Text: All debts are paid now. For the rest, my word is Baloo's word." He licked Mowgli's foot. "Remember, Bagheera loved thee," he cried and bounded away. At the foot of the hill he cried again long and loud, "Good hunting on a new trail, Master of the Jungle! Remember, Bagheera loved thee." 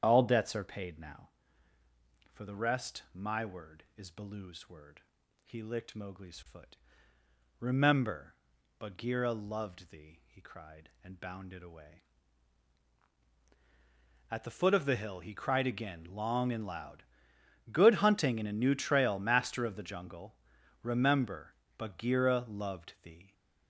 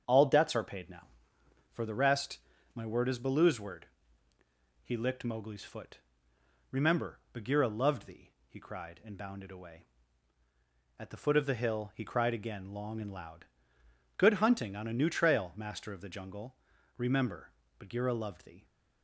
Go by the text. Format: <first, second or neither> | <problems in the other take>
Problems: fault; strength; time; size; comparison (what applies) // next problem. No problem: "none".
second | starts louder than the rest; strong; until 1.0 s; 8 dB; also in the second // says "in" for "on"; at 18.3 s